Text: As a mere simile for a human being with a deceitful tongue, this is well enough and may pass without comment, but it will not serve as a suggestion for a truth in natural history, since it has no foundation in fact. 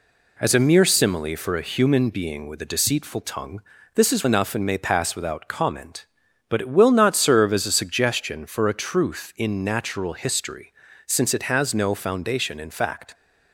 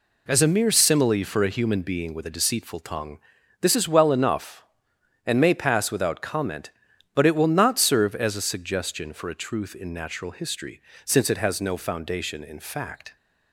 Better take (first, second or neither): second